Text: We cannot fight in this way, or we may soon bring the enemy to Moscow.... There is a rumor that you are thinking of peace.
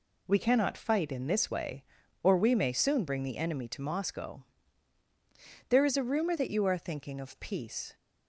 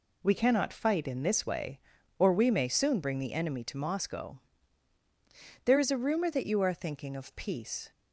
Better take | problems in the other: neither | none

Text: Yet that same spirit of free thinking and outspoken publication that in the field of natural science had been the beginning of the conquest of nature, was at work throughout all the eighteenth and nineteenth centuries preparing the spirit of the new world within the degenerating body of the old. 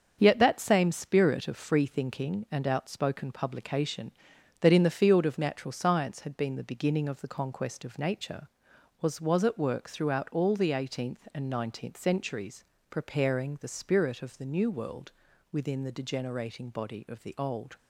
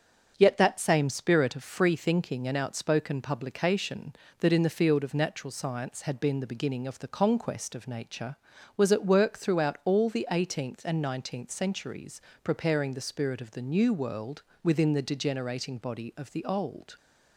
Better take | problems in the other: second | starts louder than the rest; until 1.2 s; 7 dB; also in the second // says "was" twice; at 9.2 s // pauses between "centuries" and "preparing"; slight; at 12.6 s; 0.24 s long; slight in the second // pauses between "world" and "within"; at 15.1 s; 0.40 s long; slight in the second

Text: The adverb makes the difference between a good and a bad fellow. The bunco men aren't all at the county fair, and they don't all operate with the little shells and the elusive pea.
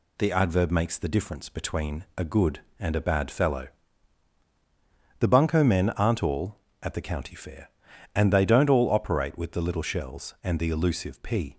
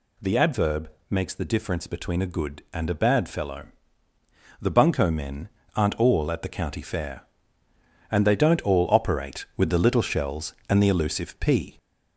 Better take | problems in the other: first | gets louder; slight; throughout; 3 dB // pauses between "adverb" and "makes"; slight; at 0.8 s; 0.22 s long // pauses between "men" and "aren't"; slight; at 5.4 s; 0.28 s long

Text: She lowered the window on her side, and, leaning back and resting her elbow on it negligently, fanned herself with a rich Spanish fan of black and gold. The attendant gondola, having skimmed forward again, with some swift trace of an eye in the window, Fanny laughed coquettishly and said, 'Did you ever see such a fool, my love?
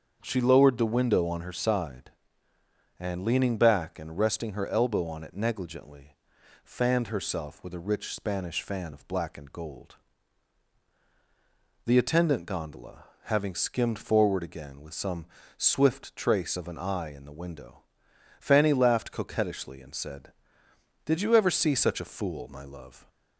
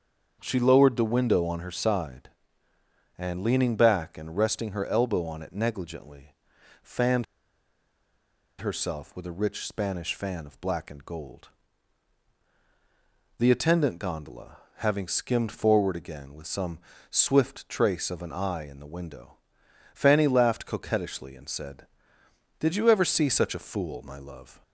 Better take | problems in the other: first | starts louder than the rest; until 1.4 s; 7 dB; also in the first // pauses between "fanned" and "herself"; strong; at 7.2 s; 1.3 s long // pauses between "some" and "swift"; slight; at 16.7 s; 0.32 s long; slight in the first

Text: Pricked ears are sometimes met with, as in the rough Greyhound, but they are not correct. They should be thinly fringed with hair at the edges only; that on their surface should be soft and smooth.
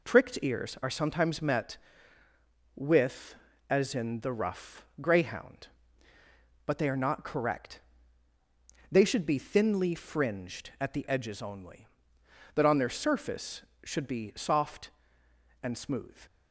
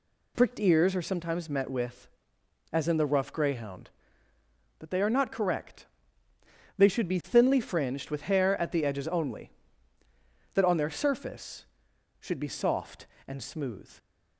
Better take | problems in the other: second | pauses between "rough" and "Greyhound"; slight; at 4.8 s; 0.16 s long // skips "with hair"; at 10.7 s

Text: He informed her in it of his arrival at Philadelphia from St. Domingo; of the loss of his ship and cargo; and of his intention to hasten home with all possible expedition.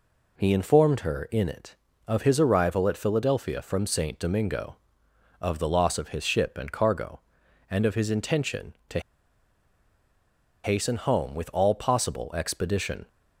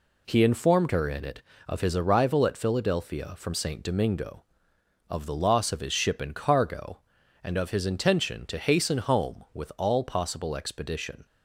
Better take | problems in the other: second | pauses between "to" and "hasten"; strong; at 8.9 s; 1.6 s long

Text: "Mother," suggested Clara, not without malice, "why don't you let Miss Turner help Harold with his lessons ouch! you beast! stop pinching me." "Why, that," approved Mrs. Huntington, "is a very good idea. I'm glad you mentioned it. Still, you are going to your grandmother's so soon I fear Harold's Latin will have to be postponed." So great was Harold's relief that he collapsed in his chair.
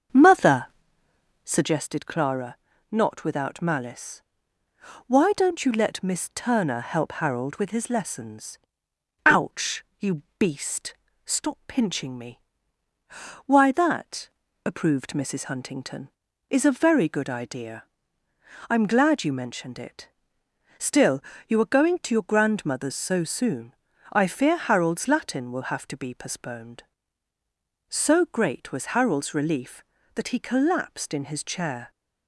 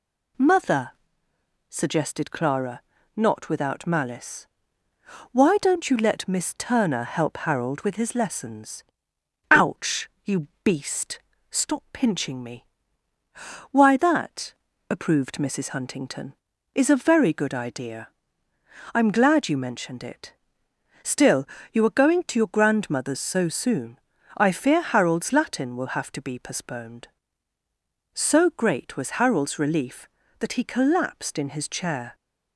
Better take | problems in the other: second | starts louder than the rest; until 1.7 s; 6.5 dB // pauses between "lessons" and "ouch"; noticeable; at 8.5 s; 0.68 s long; noticeable in the second // pauses between "you" and "beast"; slight; at 10.2 s; 0.16 s long; slight in the second // pauses between "soon" and "I"; at 23.7 s; 0.38 s long; also in the second

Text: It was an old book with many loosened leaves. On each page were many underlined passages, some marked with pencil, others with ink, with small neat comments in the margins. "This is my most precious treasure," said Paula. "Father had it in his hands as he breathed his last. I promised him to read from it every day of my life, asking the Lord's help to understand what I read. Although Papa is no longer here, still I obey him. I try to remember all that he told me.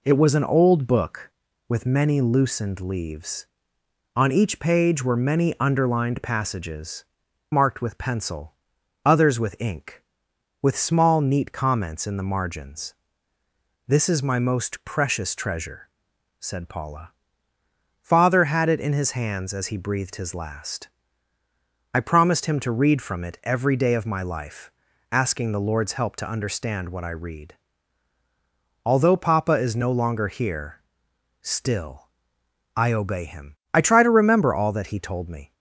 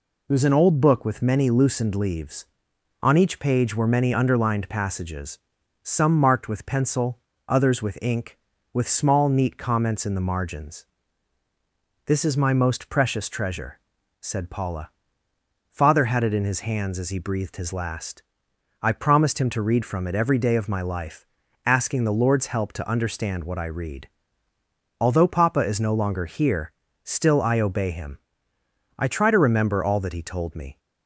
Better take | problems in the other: second | skips "some"; at 7.2 s // pauses between "still" and "I"; noticeable; at 32.0 s; 0.66 s long

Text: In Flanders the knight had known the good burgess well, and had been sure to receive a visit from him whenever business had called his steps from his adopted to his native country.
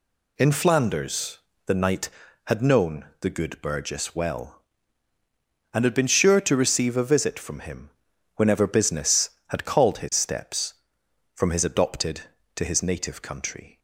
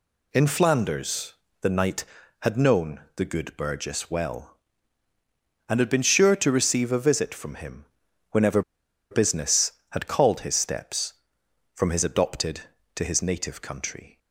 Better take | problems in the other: first | pauses between "Flanders" and "the"; slight; at 1.3 s; 0.26 s long; slight in the first // pauses between "known" and "the"; slight; at 3.0 s; 0.16 s long; slight in the first // pauses between "him" and "whenever"; noticeable; at 7.8 s; 0.48 s long; noticeable in the first // pauses between "whenever" and "business"; noticeable; at 8.6 s; 0.49 s long

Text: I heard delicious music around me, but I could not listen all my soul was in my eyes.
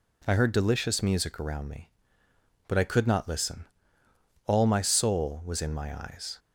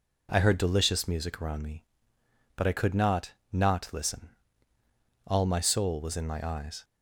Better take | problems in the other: first | says "not" twice; at 3.5 s // pauses between "listen" and "all"; noticeable; at 4.2 s; 0.96 s long; noticeable in the first

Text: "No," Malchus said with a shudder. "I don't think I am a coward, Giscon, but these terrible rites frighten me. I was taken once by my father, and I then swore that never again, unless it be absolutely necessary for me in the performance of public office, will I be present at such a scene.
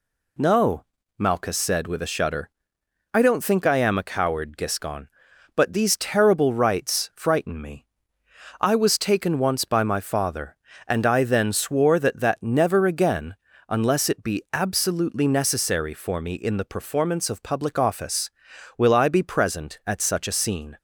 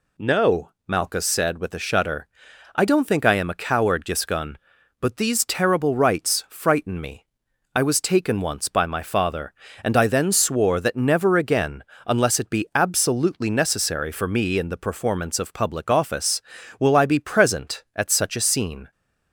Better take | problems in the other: second | says "that" twice; at 12.1 s

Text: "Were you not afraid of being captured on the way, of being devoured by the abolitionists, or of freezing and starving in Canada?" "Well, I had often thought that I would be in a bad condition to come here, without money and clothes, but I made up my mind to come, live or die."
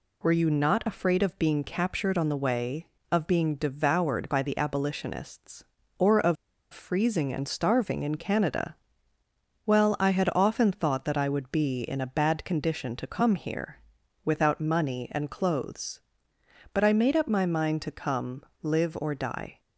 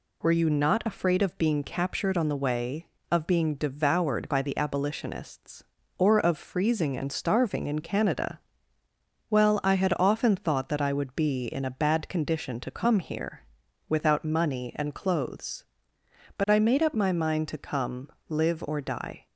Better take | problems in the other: second | pauses between "of" and "freezing"; at 6.3 s; 0.37 s long

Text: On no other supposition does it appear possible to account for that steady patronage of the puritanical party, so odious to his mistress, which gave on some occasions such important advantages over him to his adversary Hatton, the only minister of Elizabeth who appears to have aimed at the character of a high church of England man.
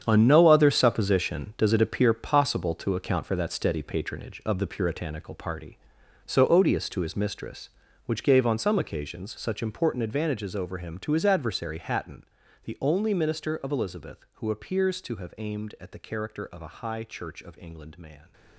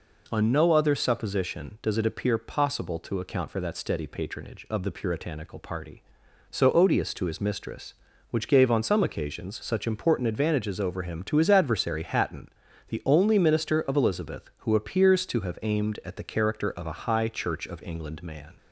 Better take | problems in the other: second | gets quieter; strong; throughout; 12.5 dB

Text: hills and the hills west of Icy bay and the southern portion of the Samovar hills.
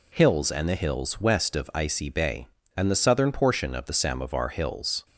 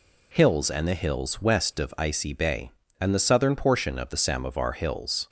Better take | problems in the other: neither | none

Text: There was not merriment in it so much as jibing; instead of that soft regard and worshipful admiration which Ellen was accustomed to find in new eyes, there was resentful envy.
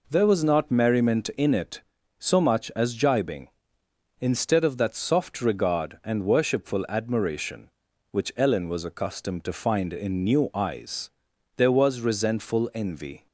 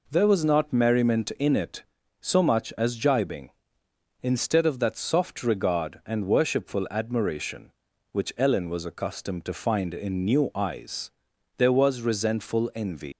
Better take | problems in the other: first | leaves "envy" unfinished; at 13.1 s; 150 ms

